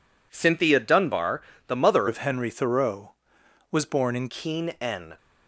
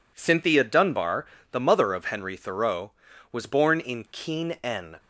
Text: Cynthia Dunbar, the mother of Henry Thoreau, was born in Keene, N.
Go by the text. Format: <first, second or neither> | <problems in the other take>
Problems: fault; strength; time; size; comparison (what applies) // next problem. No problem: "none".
second | changes voice from "of" to "in"; from 2.0 to 4.2 s; 2.2 s long